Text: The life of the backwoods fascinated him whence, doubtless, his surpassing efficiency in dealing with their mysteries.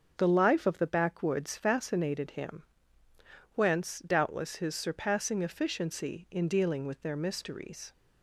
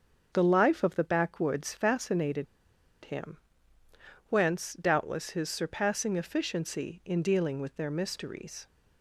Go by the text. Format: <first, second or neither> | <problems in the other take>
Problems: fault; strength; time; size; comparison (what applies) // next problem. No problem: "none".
first | starts louder than the rest; strong; until 1.3 s; 7.5 dB; strong in the first // pauses between "fascinated" and "him"; noticeable; at 2.4 s; 0.60 s long // pauses between "him" and "whence"; noticeable; at 3.3 s; 0.94 s long; noticeable in the first